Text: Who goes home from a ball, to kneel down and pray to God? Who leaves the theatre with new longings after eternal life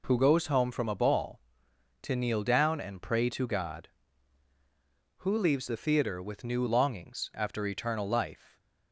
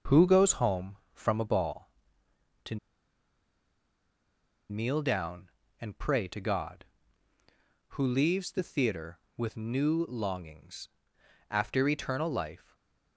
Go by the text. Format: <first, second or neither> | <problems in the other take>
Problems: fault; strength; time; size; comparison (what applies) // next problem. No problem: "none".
first | starts louder than the rest; noticeable; until 1.2 s; 6 dB // pauses between "to" and "kneel"; strong; at 2.7 s; 1.9 s long // pauses between "longings" and "after"; noticeable; at 10.8 s; 0.60 s long // stays silent after the last word; slight; from 12.5 s on; 0.6 s long